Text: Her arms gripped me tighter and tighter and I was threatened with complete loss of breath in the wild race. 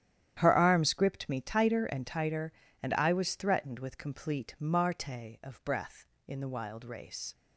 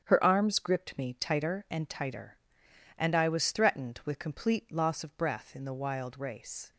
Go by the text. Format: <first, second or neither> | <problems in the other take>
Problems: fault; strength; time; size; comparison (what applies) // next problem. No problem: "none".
second | starts louder than the rest; strong; until 1.3 s; 10.5 dB; strong in the second // says "marte" for "loss"; at 4.5 s